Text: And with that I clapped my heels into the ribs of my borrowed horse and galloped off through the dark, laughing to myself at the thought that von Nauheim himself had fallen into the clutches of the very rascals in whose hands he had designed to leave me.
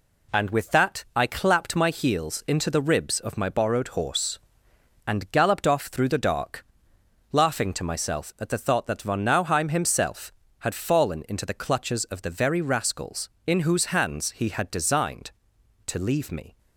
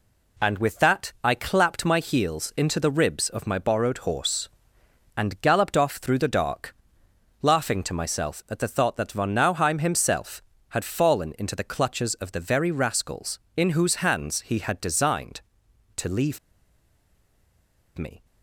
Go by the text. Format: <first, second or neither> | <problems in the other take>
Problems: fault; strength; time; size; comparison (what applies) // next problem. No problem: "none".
first | pauses between "leave" and "me"; strong; at 16.3 s; 1.5 s long